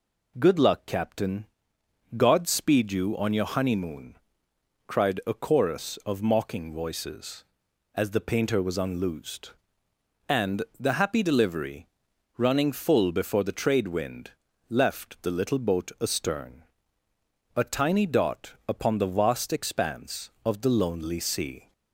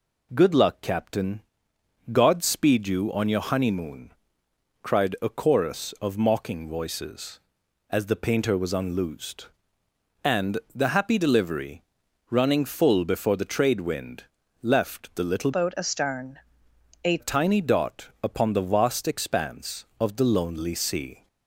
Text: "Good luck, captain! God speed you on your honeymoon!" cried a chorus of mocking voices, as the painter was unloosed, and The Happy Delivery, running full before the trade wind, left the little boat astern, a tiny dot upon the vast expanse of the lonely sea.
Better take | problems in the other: first | changes voice from "boat" to "a"; from 15.5 to 17.1 s; 1.6 s long

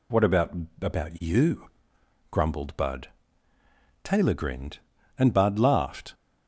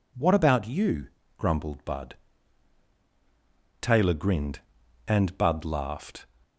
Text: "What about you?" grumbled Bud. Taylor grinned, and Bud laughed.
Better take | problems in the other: second | says "about" twice; at 0.8 s

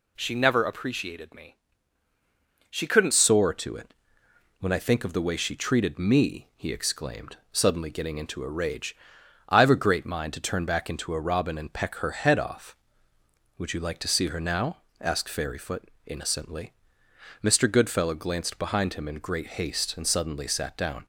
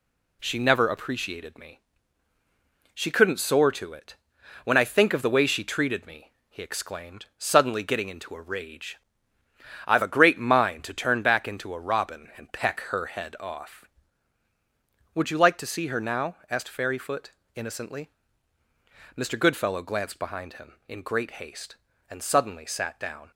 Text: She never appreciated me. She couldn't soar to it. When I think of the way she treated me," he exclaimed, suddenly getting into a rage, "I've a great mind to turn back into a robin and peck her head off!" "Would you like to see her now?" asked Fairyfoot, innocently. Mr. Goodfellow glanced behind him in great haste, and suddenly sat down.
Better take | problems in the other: second | changes voice at "soar"; from 3.1 s on; 17.9 s long

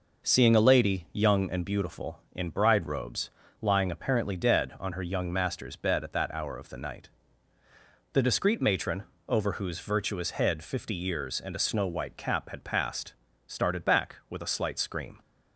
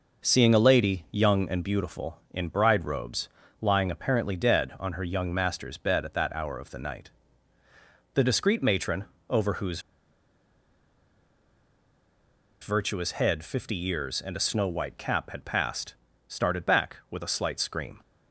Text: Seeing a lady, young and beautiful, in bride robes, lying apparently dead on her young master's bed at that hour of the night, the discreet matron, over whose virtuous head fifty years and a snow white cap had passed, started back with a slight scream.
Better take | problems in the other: first | pauses between "whose" and "virtuous"; strong; at 9.8 s; 2.8 s long

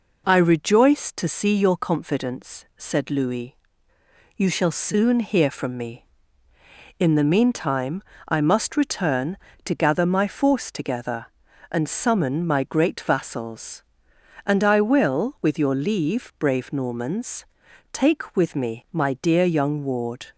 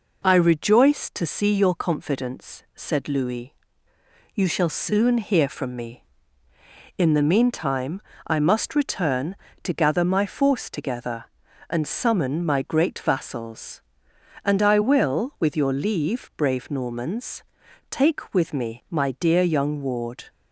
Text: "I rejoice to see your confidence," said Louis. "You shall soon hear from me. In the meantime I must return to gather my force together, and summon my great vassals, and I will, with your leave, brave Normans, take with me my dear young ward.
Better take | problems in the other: neither | pauses between "meantime" and "I"; slight; the same in both

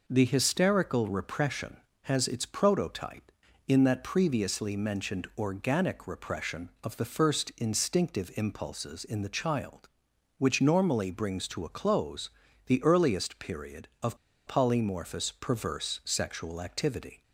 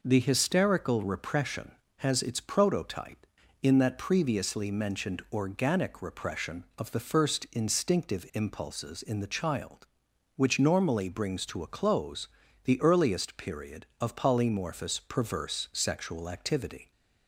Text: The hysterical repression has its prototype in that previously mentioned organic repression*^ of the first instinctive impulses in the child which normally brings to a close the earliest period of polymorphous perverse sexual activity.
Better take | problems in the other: second | pauses between "close" and "the"; at 12.2 s; 0.38 s long; also in the second // pauses between "of" and "polymorphous"; slight; at 14.1 s; 0.31 s long

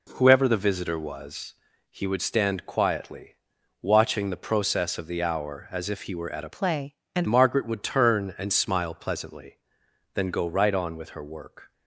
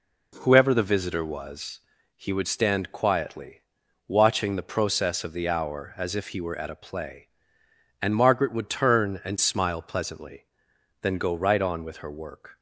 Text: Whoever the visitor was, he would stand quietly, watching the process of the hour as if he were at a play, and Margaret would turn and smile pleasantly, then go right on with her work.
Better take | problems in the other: second | changes voice from "play" to "and"; from 6.5 to 7.2 s; 0.7 s long

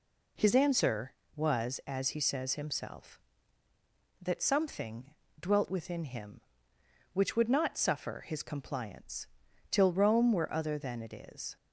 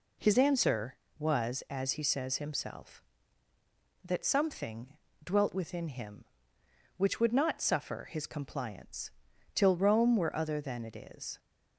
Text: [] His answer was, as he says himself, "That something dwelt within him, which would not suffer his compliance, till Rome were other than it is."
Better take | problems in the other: neither | pauses between "something" and "dwelt"; slight; the same in both

